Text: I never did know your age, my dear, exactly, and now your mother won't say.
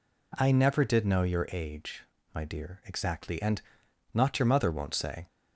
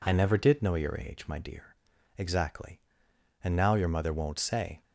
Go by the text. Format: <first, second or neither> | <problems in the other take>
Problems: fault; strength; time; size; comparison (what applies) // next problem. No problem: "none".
second | says "not" for "now"; at 4.1 s